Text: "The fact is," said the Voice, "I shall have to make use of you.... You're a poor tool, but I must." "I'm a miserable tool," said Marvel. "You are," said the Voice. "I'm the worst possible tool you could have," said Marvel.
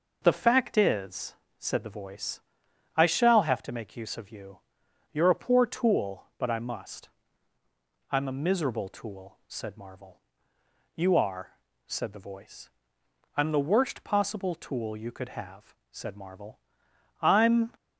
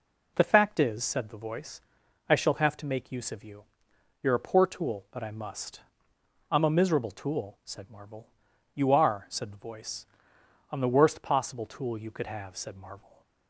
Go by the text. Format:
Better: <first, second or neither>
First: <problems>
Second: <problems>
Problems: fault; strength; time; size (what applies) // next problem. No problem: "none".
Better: second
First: goes on to say "I'm"; from 17.2 s on; 0.52 s long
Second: none